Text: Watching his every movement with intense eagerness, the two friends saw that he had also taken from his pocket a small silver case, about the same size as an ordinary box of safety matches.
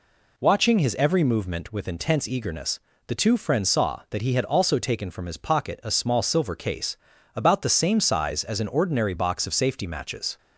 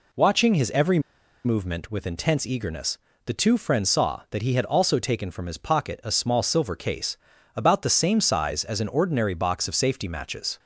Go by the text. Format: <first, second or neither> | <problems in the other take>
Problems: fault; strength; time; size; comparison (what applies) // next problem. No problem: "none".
first | pauses between "every" and "movement"; at 0.9 s; 0.45 s long